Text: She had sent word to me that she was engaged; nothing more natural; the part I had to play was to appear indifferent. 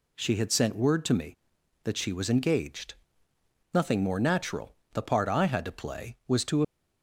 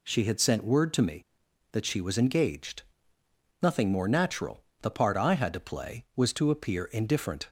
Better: second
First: stops before "appear indifferent"; at 6.6 s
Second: none

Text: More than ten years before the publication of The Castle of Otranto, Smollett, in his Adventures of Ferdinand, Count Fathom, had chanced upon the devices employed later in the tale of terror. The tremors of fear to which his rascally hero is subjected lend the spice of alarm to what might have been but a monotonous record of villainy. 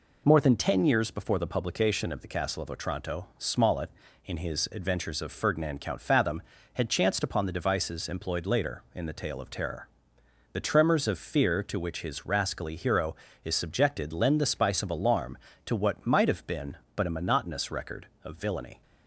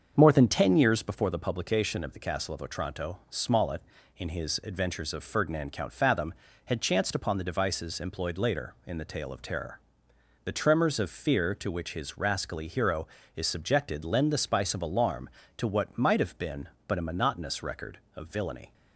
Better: first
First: none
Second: starts louder than the rest; until 1.3 s; 6.5 dB

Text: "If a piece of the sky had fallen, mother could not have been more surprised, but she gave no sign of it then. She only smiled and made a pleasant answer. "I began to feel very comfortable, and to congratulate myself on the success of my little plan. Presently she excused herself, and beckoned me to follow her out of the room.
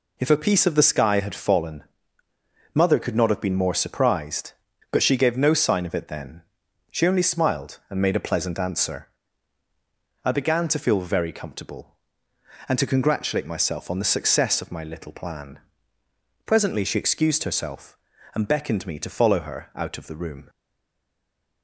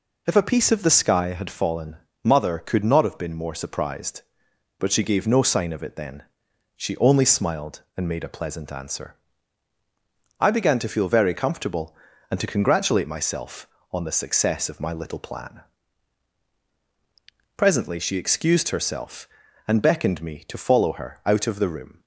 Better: second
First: stays silent after the last word; from 20.4 s on; 1.2 s long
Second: none

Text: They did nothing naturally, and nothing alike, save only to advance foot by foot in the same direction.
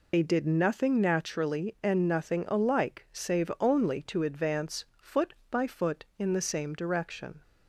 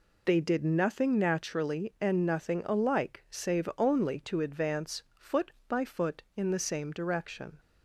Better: second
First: loses the start of "They"; at 0.1 s; 40 ms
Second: none

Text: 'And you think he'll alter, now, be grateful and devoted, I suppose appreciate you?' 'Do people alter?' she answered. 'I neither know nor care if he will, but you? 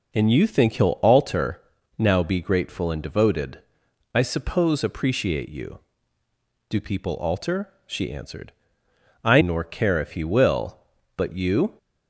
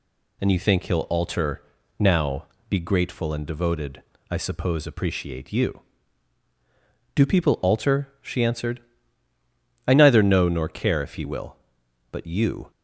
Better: second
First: skips "neither know"; at 9.4 s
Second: none

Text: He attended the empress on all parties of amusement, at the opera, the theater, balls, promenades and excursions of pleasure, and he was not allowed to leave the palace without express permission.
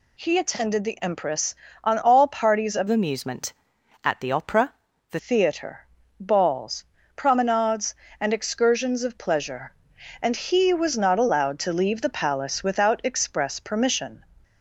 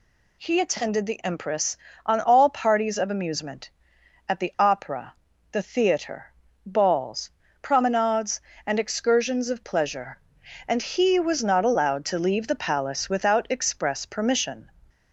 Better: second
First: changes voice from "amusement" to "the"; from 2.8 to 5.1 s; 2.3 s long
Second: none

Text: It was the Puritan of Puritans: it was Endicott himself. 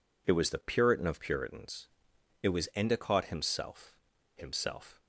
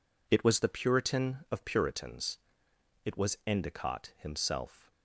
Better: second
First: says "himself" twice; at 4.3 s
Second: none

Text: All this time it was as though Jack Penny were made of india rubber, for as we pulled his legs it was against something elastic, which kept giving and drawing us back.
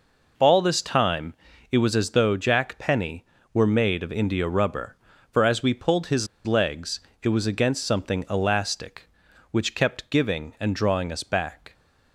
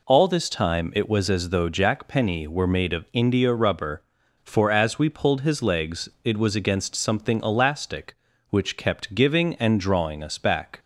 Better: second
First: pauses between "time" and "it"; at 1.3 s; 0.38 s long // pauses between "his" and "legs"; slight; at 6.2 s; 0.19 s long // pauses between "legs" and "it"; slight; at 6.9 s; 0.24 s long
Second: pauses between "legs" and "it"; slight; at 6.0 s; 0.16 s long

